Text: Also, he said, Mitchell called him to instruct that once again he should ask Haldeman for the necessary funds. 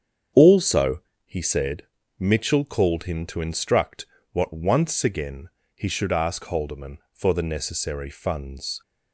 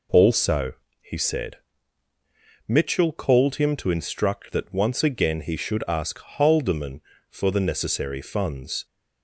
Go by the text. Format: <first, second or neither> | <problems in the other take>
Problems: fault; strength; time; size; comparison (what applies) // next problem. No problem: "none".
second | starts louder than the rest; strong; until 1.6 s; 8 dB // says "what" for "that"; at 4.3 s // pauses between "again" and "he"; slight; at 5.4 s; 0.26 s long